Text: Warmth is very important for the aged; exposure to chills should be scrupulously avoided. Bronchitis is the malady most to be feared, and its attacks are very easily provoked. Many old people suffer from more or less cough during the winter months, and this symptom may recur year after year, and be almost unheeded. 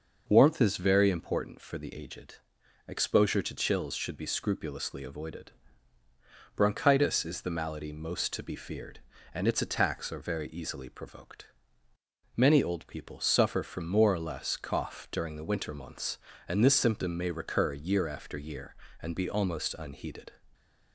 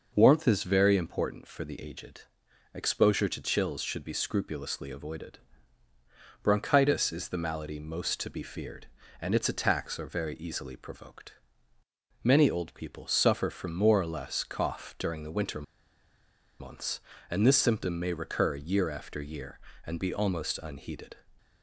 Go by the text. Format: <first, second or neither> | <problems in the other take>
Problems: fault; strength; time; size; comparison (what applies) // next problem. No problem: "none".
first | pauses between "winter" and "months"; noticeable; at 15.6 s; 0.97 s long